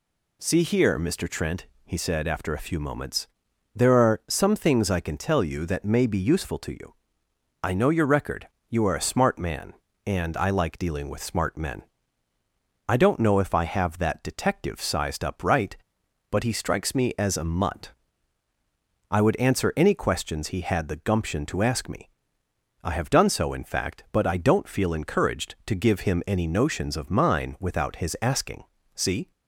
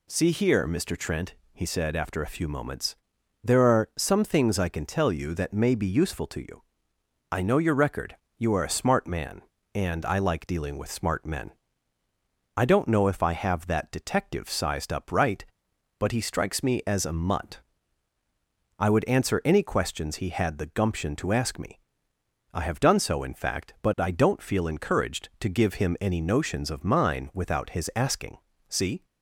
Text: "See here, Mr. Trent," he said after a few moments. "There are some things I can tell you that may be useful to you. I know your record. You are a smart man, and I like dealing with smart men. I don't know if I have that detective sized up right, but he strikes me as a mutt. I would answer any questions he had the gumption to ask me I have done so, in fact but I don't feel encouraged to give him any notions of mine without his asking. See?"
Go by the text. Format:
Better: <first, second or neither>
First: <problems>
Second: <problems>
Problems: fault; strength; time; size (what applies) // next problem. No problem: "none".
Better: neither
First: pauses between "me" and "I"; noticeable; at 22.1 s; 0.70 s long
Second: pauses between "me" and "I"; noticeable; at 21.8 s; 0.70 s long